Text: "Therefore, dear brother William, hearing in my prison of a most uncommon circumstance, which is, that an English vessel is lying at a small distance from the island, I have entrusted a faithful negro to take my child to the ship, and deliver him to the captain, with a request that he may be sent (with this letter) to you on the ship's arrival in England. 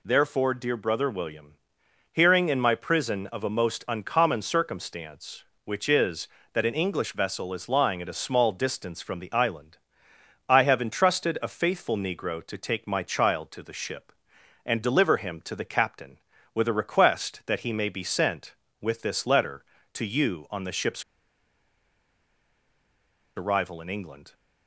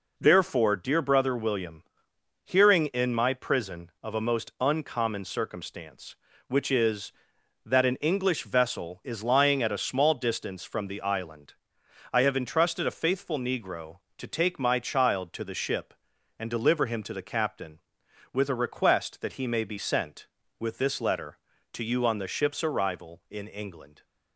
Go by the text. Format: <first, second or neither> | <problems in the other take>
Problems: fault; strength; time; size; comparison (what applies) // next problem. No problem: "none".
second | pauses between "ship's" and "arrival"; strong; at 21.0 s; 2.3 s long